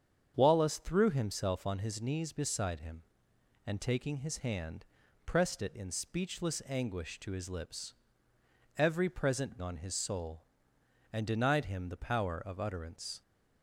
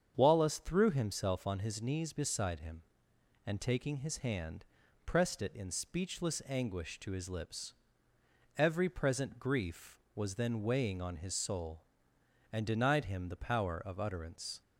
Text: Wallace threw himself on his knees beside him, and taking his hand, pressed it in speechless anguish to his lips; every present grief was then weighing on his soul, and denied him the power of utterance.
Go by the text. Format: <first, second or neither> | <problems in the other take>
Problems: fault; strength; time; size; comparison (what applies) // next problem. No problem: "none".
second | starts louder than the rest; strong; until 1.3 s; 7.5 dB; strong in the second // skips "grief was then weighing"; at 9.6 s